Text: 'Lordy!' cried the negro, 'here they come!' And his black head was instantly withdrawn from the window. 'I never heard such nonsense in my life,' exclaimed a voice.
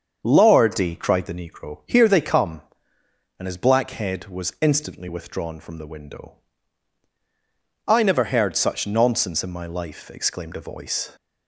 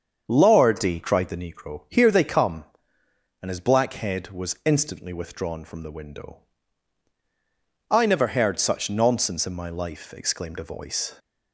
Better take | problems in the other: neither | starts louder than the rest; the same in both

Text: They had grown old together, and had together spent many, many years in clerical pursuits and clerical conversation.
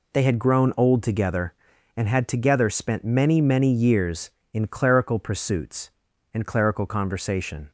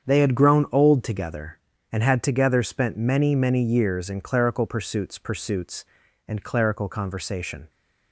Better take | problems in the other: first | starts louder than the rest; strong; until 1.1 s; 8 dB // says "pursuits" twice; at 5.1 s

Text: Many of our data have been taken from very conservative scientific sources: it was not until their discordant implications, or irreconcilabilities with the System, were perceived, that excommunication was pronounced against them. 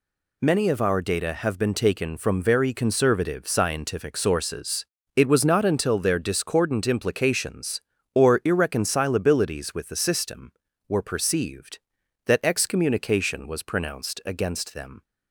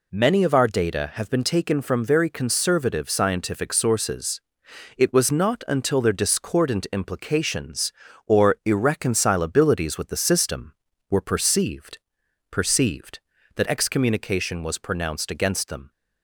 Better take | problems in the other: first | says "perceived" twice; at 12.4 s

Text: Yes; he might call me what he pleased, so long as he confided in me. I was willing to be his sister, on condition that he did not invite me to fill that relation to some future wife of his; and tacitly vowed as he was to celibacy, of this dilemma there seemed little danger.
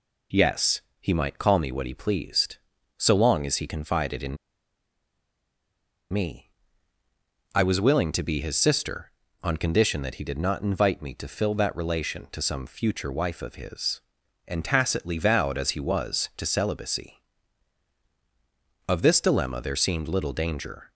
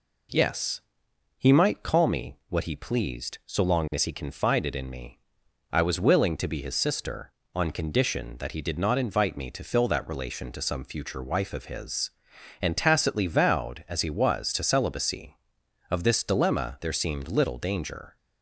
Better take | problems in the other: second | pauses between "in" and "me"; strong; at 4.3 s; 1.7 s long

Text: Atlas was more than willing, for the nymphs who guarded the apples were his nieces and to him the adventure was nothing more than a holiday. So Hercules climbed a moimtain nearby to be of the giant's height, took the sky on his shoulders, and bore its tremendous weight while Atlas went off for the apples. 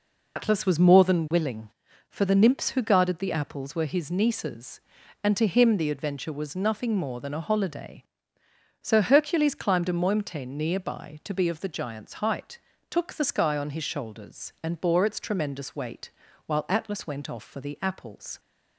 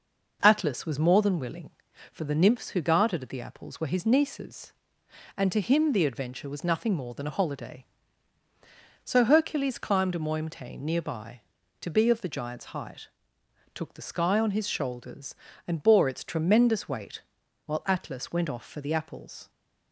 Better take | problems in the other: second | loses the start of "Atlas"; at 0.3 s; 90 ms // pauses between "weight" and "while"; slight; at 16.1 s; 0.34 s long; also in the second

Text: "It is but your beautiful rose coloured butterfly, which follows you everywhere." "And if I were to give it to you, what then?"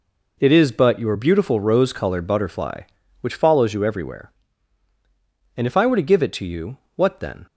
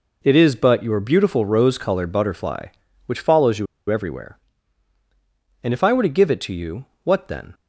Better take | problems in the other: first | pauses between "you" and "everywhere"; slight; at 3.6 s; 0.24 s long

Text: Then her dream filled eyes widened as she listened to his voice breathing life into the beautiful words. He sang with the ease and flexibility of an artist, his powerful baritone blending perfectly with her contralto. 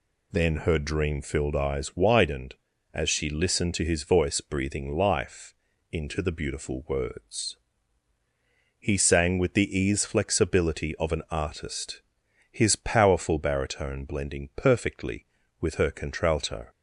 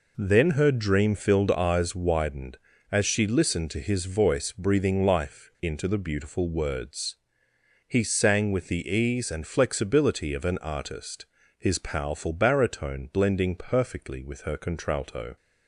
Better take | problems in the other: second | pauses between "life" and "into"; at 5.5 s; 0.38 s long // skips "and"; at 10.0 s

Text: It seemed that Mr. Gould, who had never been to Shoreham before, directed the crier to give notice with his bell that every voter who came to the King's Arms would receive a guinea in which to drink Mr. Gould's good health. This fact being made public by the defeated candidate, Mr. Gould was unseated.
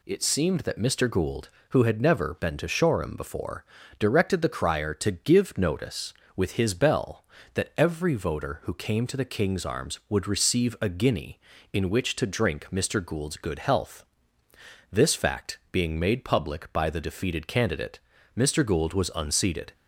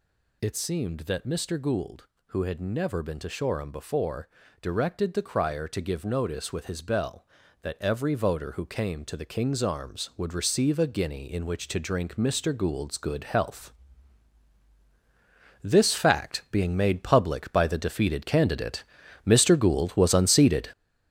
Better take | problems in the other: first | gets louder; strong; throughout; 8.5 dB

